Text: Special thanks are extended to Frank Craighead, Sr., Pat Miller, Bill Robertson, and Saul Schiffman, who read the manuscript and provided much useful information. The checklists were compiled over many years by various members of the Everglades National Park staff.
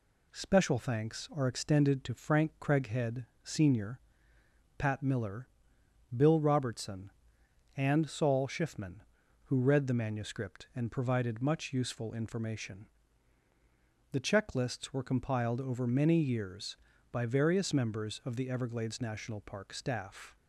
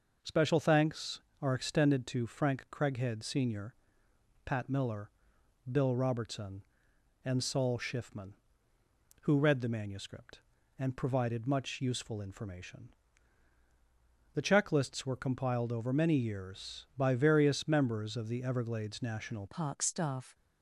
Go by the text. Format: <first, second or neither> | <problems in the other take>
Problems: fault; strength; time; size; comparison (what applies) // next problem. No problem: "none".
first | changes voice at "Park"; from 19.4 s on; 0.9 s long